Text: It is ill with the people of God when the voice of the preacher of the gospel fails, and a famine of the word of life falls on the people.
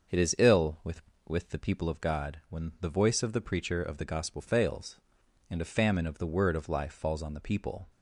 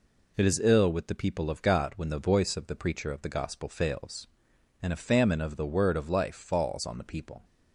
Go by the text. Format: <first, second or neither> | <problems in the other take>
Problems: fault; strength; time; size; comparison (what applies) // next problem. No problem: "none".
second | starts louder than the rest; until 1.4 s; 6.5 dB // says "with" twice; at 1.2 s